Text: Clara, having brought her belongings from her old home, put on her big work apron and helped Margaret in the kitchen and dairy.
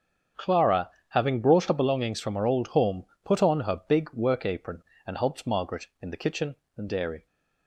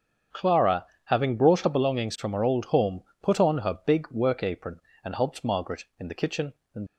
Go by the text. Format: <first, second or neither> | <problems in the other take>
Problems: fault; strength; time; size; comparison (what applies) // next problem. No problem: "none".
first | starts louder than the rest; strong; until 1.5 s; 7.5 dB; strong in the first // stops before "dairy"; at 6.8 s